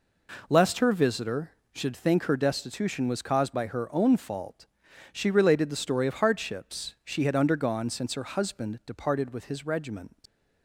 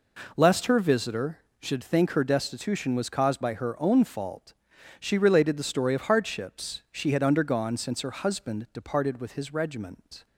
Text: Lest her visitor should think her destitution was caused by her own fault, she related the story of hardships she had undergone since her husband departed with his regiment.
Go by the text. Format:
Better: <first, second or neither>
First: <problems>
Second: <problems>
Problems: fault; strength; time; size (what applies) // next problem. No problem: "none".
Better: second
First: leaves "regiment" unfinished; at 10.2 s; 125 ms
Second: none